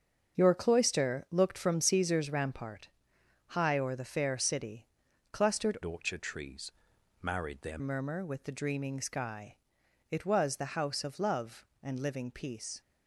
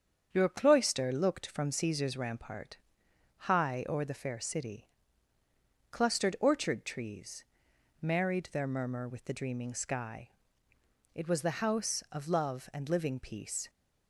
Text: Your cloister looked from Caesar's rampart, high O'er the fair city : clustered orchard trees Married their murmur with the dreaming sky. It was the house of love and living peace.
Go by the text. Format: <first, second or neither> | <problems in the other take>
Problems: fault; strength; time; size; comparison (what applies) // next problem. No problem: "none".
second | starts louder than the rest; until 1.4 s; 7 dB; strong in the second // changes voice from "orchard" to "their"; from 5.8 to 7.7 s; 1.9 s long // pauses between "trees" and "Married"; noticeable; at 6.7 s; 0.52 s long; noticeable in the second